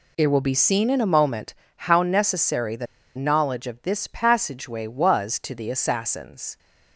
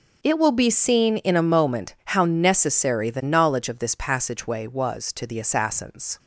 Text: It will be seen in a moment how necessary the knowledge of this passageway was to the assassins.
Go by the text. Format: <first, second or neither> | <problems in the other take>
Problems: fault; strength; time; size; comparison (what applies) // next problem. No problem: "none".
second | pauses between "moment" and "how"; slight; at 1.5 s; 0.20 s long // pauses between "the" and "knowledge"; slight; at 2.8 s; 0.30 s long